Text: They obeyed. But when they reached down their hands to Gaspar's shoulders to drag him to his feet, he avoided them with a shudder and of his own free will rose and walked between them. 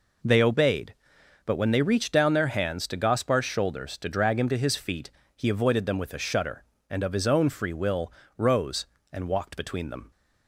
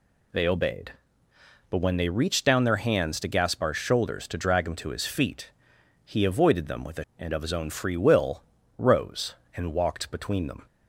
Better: first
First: pauses between "will" and "rose"; slight; at 8.1 s; 0.26 s long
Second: skips "shudder"; at 7.1 s // pauses between "will" and "rose"; slight; at 8.4 s; 0.36 s long

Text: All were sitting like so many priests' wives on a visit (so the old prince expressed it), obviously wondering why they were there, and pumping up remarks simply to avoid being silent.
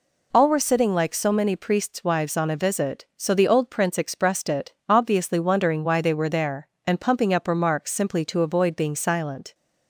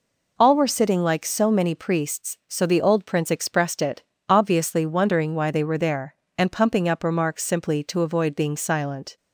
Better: first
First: none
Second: skips "wives on a visit"; at 2.4 s

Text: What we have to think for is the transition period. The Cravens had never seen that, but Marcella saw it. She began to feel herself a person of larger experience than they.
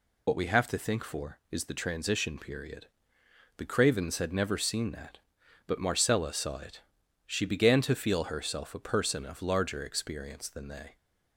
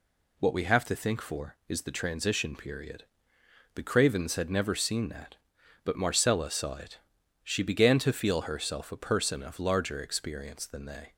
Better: second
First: loses the start of "What"; at 0.2 s; 60 ms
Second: none

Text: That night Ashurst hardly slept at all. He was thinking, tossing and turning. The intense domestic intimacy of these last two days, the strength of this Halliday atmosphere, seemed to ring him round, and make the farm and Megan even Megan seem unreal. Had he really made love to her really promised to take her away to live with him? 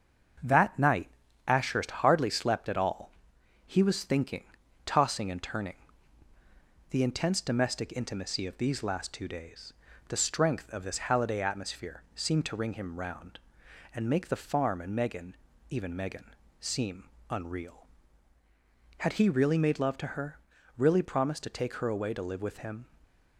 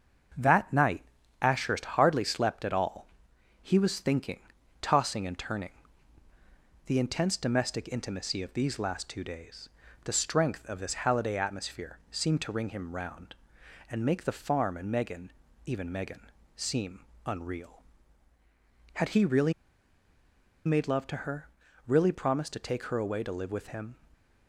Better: first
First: starts louder than the rest; until 1.8 s; 6.5 dB // pauses between "night" and "Ashurst"; at 1.0 s; 0.38 s long // pauses between "Megan" and "even"; slight; at 15.3 s; 0.34 s long // pauses between "Megan" and "seem"; slight; at 16.3 s; 0.28 s long // pauses between "seem" and "unreal"; slight; at 17.0 s; 0.24 s long // pauses between "her" and "really"; at 20.3 s; 0.40 s long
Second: starts louder than the rest; until 1.7 s; 6.5 dB // pauses between "night" and "Ashurst"; at 1.0 s; 0.38 s long // pauses between "Megan" and "even"; slight; at 15.3 s; 0.34 s long // pauses between "Megan" and "seem"; slight; at 16.2 s; 0.28 s long // pauses between "seem" and "unreal"; slight; at 17.0 s; 0.24 s long // pauses between "really" and "made"; at 19.5 s; 1.1 s long // pauses between "her" and "really"; at 21.4 s; 0.40 s long

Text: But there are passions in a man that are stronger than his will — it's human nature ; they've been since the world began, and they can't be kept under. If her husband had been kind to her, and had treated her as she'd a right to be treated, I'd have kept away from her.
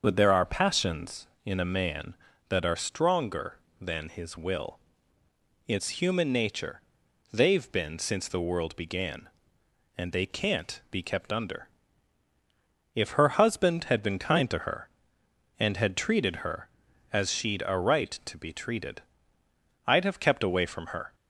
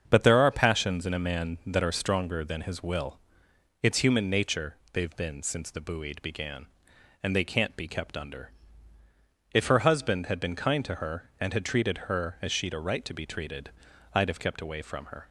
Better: first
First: starts louder than the rest; until 1.0 s; 6.5 dB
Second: starts louder than the rest; until 1.0 s; 7 dB // says "buoyed" for "world"; at 5.8 s

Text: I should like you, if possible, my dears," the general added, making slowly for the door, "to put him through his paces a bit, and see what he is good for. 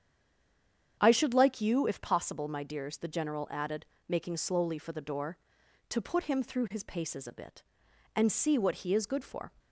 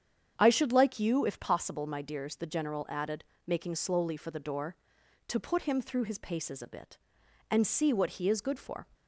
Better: second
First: stays silent before the first word; until 0.9 s; 0.9 s long // starts louder than the rest; strong; until 2.0 s; 8.5 dB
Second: starts louder than the rest; strong; until 1.3 s; 8.5 dB

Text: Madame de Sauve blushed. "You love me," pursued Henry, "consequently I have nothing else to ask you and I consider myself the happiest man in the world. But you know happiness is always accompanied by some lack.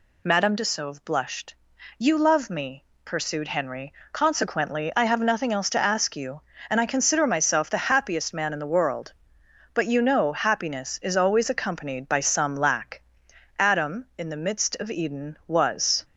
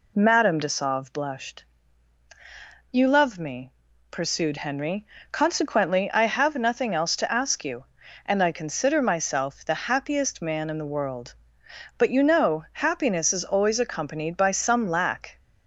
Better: second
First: goes on to say "Adam in the midst of Eden was"; strong; from 13.5 s on; 2.4 s long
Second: none

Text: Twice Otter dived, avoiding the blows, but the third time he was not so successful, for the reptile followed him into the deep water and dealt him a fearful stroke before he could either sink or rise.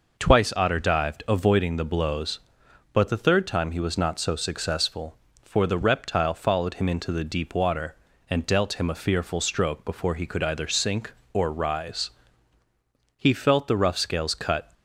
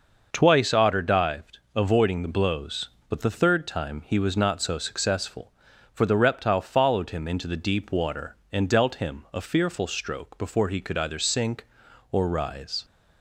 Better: second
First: goes on to say "He felt the rough scales cut"; from 13.1 s on; 1.5 s long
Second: none

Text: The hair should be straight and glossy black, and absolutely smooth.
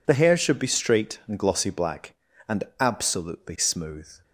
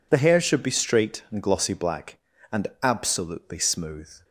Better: neither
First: pauses between "and" and "absolutely"; slight; at 2.6 s; 0.16 s long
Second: pauses between "and" and "absolutely"; slight; at 2.6 s; 0.15 s long

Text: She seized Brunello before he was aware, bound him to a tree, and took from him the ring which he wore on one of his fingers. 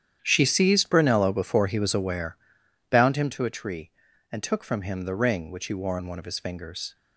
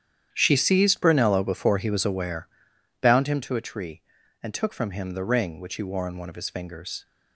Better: neither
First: starts louder than the rest; strong; until 1.2 s; 9.5 dB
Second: starts louder than the rest; strong; until 1.3 s; 9.5 dB

